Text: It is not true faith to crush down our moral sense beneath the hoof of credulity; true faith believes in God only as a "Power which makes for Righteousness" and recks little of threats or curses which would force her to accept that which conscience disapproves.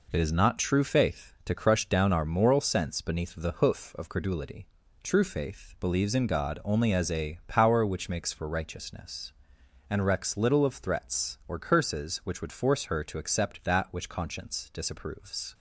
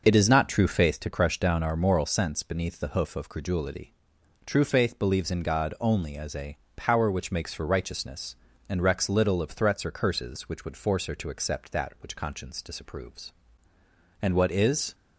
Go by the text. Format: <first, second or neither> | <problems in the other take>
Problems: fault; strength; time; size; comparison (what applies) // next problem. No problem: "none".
first | starts louder than the rest; noticeable; until 1.0 s; 6 dB // pauses between "a" and "Power"; slight; at 6.5 s; 0.18 s long // goes on to say "And what is"; noticeable; from 14.2 s on; 0.74 s long